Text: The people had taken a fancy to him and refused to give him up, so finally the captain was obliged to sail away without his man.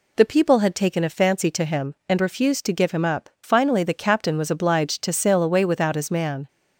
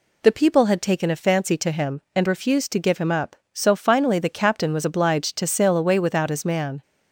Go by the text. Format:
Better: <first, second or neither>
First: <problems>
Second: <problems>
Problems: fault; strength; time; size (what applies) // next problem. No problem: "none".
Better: second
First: skips "so"; at 3.3 s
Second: none